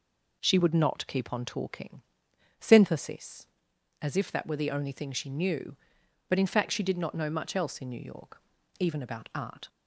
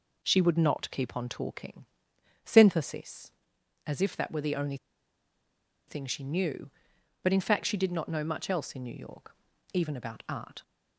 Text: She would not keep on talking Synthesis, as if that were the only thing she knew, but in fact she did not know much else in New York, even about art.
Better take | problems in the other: first | pauses between "talking" and "Synthesis"; noticeable; at 1.8 s; 0.60 s long; noticeable in the first // pauses between "only" and "thing"; at 4.7 s; 1.1 s long

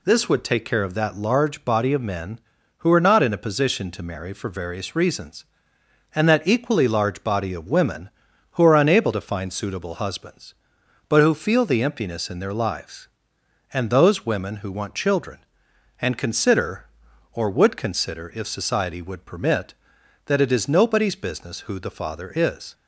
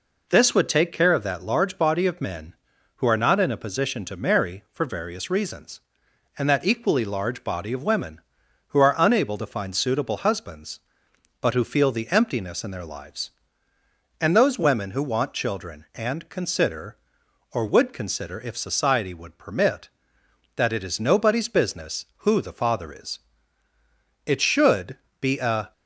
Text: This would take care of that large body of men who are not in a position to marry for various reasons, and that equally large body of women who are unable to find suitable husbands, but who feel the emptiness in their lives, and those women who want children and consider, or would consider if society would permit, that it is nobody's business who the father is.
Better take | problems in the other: first | goes on to say "It should be a"; from 24.2 s on; 1.4 s long

